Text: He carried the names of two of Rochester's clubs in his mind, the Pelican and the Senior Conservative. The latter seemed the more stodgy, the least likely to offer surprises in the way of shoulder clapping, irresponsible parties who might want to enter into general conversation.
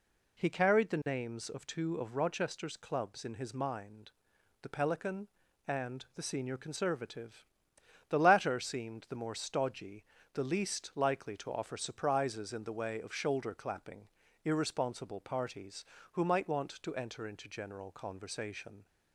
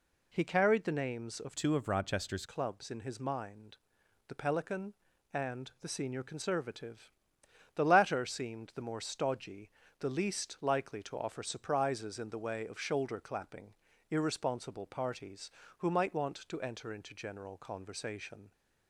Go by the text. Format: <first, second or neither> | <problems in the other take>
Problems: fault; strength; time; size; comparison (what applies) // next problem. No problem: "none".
first | changes voice from "two" to "Rochester's"; from 1.5 to 2.4 s; 0.9 s long